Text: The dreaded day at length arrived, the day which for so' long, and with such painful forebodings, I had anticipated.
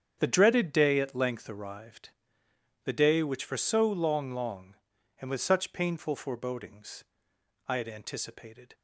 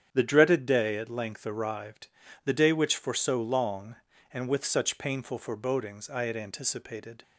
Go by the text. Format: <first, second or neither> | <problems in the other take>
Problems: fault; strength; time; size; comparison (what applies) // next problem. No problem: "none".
second | starts louder than the rest; strong; until 1.2 s; 8 dB; strong in the second // says "long" twice; at 4.3 s